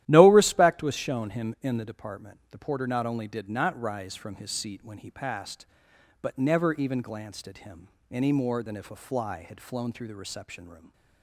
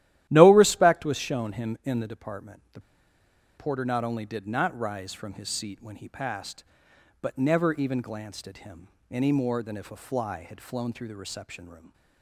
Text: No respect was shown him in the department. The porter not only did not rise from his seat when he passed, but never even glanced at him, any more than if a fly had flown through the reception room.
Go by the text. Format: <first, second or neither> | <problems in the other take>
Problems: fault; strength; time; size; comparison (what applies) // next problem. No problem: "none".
first | starts louder than the rest; strong; until 1.3 s; 13.5 dB; strong in the first // pauses between "The" and "porter"; noticeable; at 2.7 s; 0.77 s long